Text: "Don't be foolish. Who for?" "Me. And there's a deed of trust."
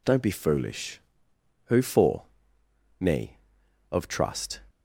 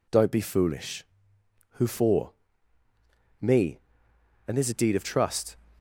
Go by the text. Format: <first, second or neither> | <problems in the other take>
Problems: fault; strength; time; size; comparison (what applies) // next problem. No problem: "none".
second | skips "And there's a deed"; at 3.6 s